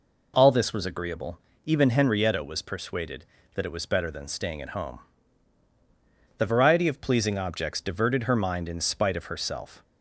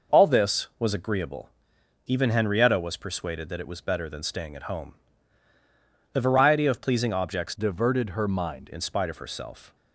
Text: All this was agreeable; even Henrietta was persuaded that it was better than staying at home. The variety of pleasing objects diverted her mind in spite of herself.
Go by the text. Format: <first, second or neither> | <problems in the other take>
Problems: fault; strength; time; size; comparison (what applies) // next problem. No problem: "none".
first | changes voice from "diverted" to "mind"; from 7.5 to 8.6 s; 1.1 s long